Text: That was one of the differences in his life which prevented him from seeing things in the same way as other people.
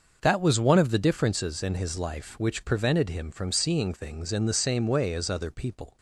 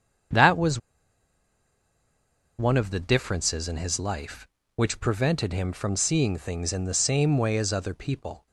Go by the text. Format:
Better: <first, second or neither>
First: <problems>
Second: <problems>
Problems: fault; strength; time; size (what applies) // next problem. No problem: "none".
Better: first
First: starts louder than the rest; until 1.2 s; 6 dB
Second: starts louder than the rest; strong; until 3.1 s; 7.5 dB // pauses between "was" and "one"; strong; at 0.7 s; 1.7 s long